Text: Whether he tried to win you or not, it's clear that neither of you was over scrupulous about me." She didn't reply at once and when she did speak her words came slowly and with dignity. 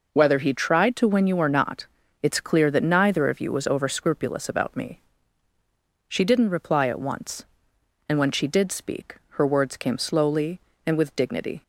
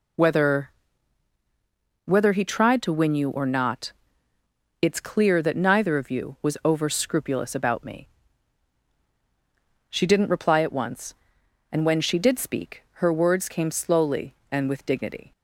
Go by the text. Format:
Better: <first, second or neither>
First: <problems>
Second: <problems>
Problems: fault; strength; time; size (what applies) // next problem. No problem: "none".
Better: first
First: none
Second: says "Whether" twice; at 2.0 s